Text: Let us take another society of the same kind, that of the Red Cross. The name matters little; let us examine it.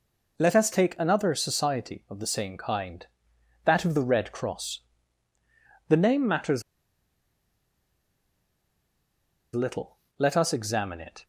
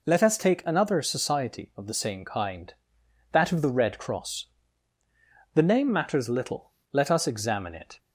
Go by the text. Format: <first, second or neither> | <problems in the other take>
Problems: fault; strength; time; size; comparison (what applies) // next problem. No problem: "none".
second | pauses between "matters" and "little"; strong; at 6.6 s; 2.9 s long